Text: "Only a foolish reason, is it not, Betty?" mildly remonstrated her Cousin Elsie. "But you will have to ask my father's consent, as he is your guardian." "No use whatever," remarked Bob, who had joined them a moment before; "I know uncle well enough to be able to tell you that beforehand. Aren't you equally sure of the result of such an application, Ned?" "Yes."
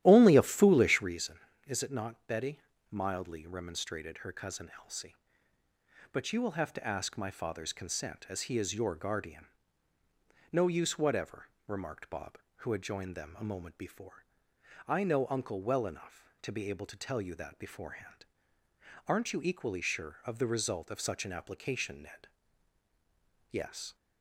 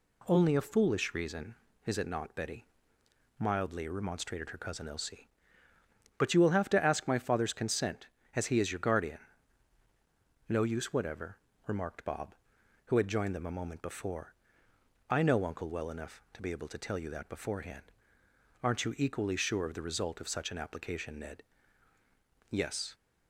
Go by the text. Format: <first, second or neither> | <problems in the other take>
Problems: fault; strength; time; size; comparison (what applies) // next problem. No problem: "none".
second | starts louder than the rest; strong; until 1.2 s; 13 dB